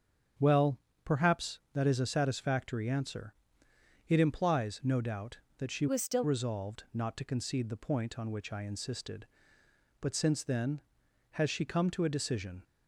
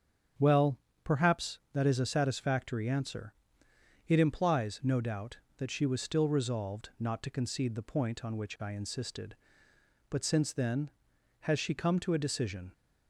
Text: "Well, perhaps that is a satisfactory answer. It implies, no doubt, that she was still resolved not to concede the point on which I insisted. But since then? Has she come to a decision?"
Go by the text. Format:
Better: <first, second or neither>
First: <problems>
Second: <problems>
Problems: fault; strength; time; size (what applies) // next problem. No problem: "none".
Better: second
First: starts louder than the rest; strong; until 1.7 s; 7.5 dB // changes voice from "was" to "still"; from 5.8 to 6.2 s; 0.4 s long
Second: starts louder than the rest; strong; until 1.7 s; 7.5 dB